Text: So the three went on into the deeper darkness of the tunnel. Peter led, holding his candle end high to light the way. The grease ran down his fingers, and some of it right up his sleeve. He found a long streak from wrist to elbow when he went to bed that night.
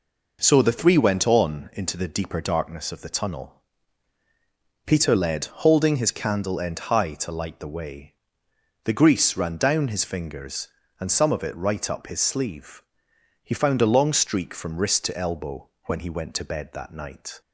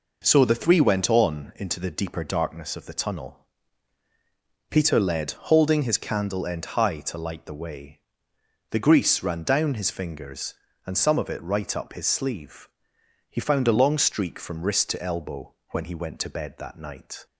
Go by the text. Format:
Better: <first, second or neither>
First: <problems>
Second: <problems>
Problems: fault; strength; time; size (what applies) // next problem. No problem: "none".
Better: neither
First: pauses between "elbow" and "when"; slight; at 15.6 s; 0.16 s long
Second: pauses between "elbow" and "when"; slight; at 15.5 s; 0.16 s long